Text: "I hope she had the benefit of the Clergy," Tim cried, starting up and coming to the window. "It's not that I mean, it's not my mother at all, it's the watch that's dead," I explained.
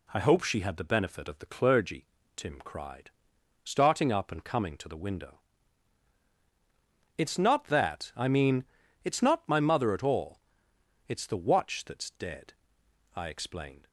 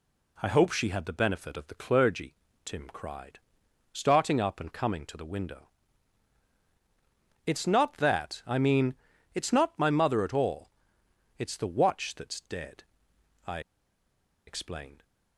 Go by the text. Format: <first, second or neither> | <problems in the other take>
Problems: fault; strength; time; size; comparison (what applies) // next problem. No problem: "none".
first | pauses between "I" and "explained"; noticeable; at 13.6 s; 0.86 s long